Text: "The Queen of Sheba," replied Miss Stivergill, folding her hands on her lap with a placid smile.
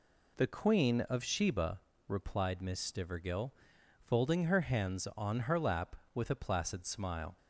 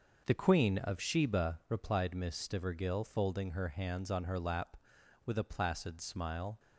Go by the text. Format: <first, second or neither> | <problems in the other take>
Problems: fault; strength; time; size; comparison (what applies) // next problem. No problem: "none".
neither | none